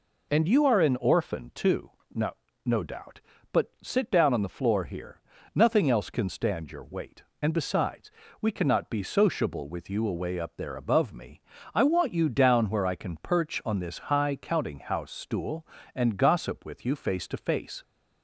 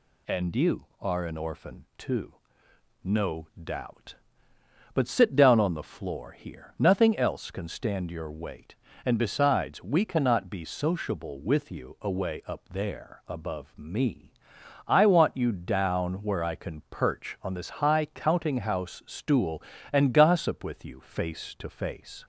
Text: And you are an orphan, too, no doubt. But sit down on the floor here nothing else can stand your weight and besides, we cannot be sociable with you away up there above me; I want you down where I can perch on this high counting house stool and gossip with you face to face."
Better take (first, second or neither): second